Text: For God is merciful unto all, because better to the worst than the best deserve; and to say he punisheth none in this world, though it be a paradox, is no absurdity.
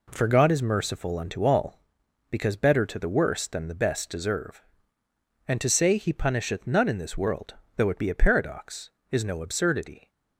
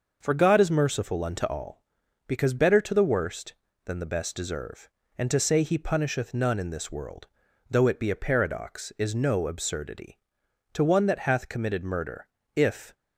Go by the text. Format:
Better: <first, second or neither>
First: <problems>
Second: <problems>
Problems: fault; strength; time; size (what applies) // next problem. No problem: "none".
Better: first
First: none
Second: starts louder than the rest; noticeable; until 1.2 s; 6 dB // goes on to say "To one that hath committed murder if"; strong; from 10.7 s on; 2.2 s long